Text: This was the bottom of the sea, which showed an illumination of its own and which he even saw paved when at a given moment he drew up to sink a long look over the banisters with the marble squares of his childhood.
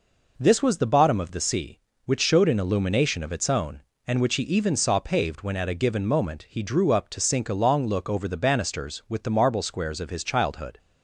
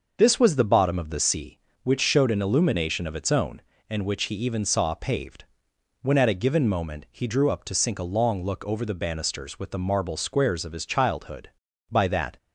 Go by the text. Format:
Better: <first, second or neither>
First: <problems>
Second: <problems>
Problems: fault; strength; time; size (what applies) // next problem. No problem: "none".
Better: first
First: none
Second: starts louder than the rest; noticeable; until 1.1 s; 6 dB // pauses between "paved" and "when"; noticeable; at 5.4 s; 0.58 s long // goes on to say "By that"; slight; from 11.8 s on; 0.48 s long